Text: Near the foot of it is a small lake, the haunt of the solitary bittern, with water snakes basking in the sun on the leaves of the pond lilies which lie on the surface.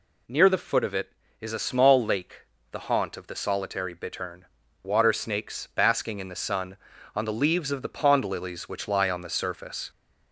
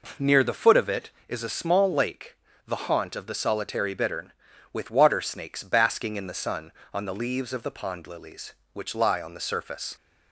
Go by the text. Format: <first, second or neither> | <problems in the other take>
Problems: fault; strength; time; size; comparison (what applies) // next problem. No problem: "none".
second | skips "with"; at 4.6 s